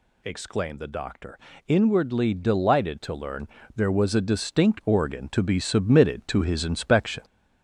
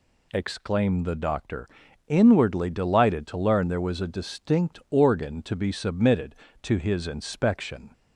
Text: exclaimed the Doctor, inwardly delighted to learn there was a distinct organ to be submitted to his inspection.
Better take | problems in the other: second | gets louder; throughout; 3.5 dB // pauses between "learn" and "there"; slight; at 3.4 s; 0.26 s long

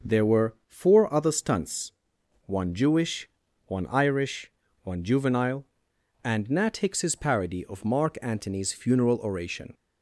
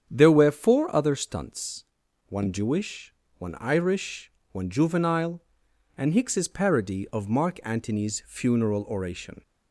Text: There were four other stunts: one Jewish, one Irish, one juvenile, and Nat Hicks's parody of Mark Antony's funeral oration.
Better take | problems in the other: first | starts louder than the rest; strong; until 1.1 s; 8.5 dB // skips "Nat"; at 6.1 s

